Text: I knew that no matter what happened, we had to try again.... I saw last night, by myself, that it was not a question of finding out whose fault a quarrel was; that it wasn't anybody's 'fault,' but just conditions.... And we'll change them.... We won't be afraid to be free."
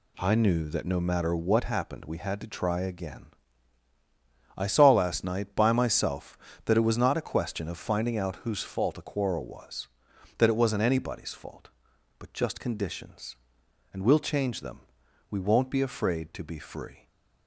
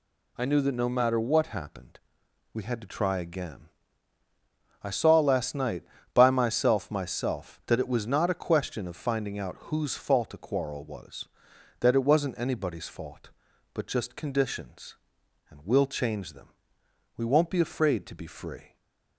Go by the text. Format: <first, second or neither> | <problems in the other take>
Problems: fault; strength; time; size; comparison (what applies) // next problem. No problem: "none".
first | says "myself" twice; at 6.9 s // stays silent after the last word; slight; from 18.6 s on; 0.5 s long